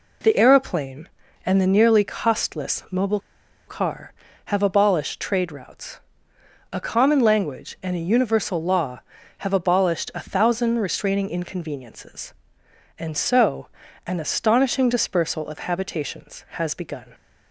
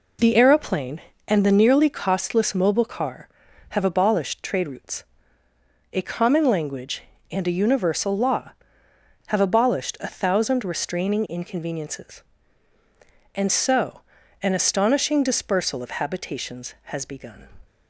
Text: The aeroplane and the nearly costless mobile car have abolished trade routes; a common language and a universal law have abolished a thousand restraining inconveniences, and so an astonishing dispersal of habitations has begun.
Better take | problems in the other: second | pauses between "mobile" and "car"; noticeable; at 3.1 s; 0.49 s long // pauses between "so" and "an"; slight; at 13.6 s; 0.36 s long; also in the second

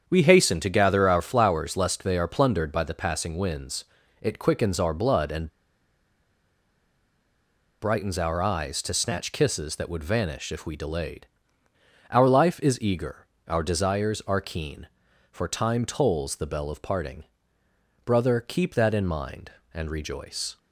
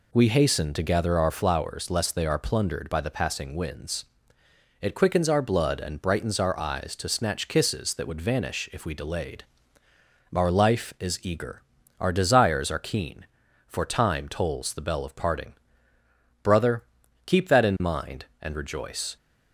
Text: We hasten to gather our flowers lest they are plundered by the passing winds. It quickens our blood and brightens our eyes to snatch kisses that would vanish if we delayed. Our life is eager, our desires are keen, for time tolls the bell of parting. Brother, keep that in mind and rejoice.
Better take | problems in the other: second | starts louder than the rest; strong; until 1.0 s; 7.5 dB // pauses between "and" and "brightens"; strong; at 5.4 s; 2.3 s long

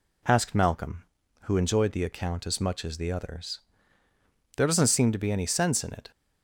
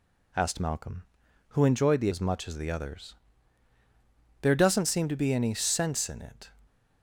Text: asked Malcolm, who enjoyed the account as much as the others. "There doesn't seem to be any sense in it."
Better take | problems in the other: first | skips "account"; at 2.0 s

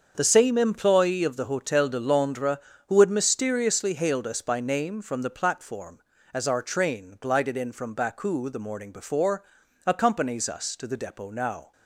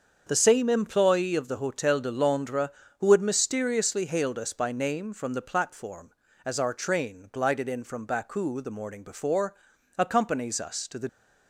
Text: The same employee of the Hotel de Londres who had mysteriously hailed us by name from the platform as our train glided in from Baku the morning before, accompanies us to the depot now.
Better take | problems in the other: first | starts louder than the rest; until 1.2 s; 7 dB; also in the first // stops before "depot now"; at 11.0 s

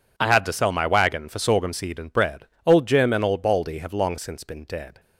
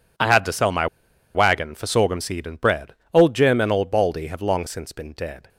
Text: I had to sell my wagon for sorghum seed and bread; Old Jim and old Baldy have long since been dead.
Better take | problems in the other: first | pauses between "my" and "wagon"; noticeable; at 0.8 s; 0.48 s long

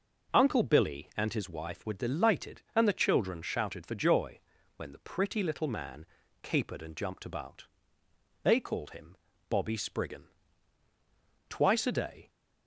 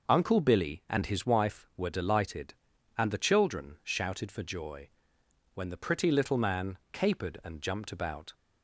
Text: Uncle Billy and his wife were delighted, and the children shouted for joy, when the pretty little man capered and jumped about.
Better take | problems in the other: second | pauses between "man" and "capered"; slight; at 6.0 s; 0.36 s long // goes on to say "They called him Bobby Spriggan Twice a day"; strong; from 8.4 s on; 3.8 s long

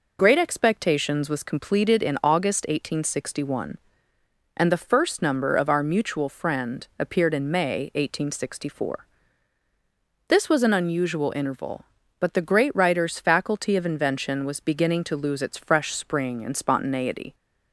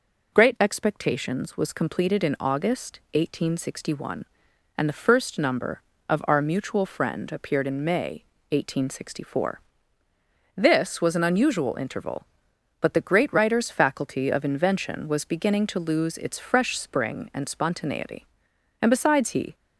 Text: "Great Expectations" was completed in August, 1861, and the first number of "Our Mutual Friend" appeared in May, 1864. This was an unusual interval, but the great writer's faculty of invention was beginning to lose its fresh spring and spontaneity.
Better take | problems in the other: first | goes on to say "And besides he"; noticeable; from 18.8 s on; 0.74 s long

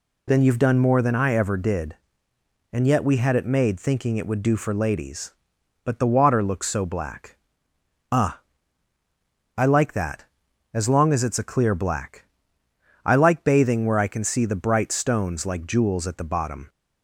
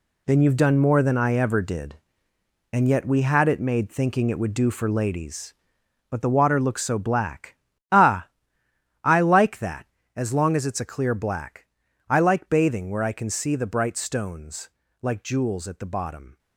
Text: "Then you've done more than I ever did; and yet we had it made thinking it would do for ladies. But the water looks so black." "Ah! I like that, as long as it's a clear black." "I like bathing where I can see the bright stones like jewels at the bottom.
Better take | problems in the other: first | gets quieter; strong; throughout; 11 dB // pauses between "stones" and "like"; slight; at 14.7 s; 0.32 s long

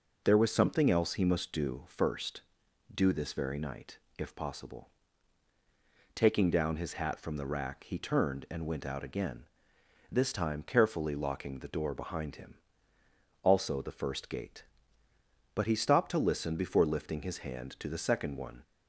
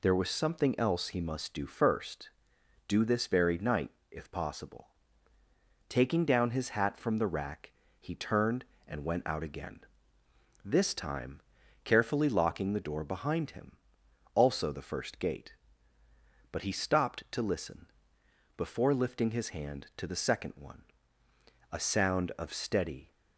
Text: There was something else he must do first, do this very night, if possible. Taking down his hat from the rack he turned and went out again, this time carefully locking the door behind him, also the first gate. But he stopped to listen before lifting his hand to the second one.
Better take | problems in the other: first | pauses between "rack" and "he"; slight; at 7.7 s; 0.28 s long // pauses between "time" and "carefully"; at 11.4 s; 0.44 s long // pauses between "listen" and "before"; noticeable; at 17.9 s; 0.66 s long // goes on to say "A sound of steady"; from 21.7 s on; 1.4 s long

